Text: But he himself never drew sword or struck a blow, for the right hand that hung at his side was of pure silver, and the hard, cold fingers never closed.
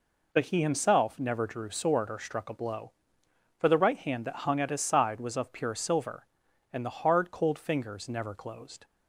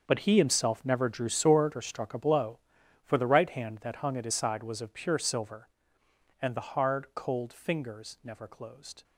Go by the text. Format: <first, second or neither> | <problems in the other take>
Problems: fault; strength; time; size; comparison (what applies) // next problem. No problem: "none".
first | gets quieter; strong; throughout; 13.5 dB